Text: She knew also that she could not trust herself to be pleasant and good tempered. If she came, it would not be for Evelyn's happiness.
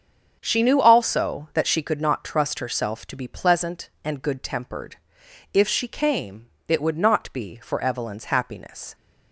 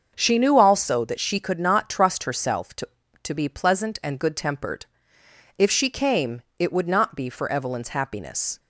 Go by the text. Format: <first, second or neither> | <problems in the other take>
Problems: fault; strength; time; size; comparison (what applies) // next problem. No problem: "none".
first | starts louder than the rest; until 1.1 s; 6.5 dB; also in the first // says "to" twice; at 3.2 s